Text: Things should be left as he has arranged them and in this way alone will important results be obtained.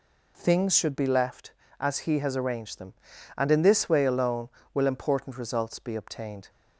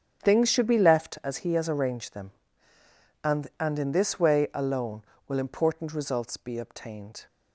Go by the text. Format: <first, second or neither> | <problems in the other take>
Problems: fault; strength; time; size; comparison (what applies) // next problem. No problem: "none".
first | starts louder than the rest; strong; until 1.2 s; 8 dB // says "and" twice; at 3.5 s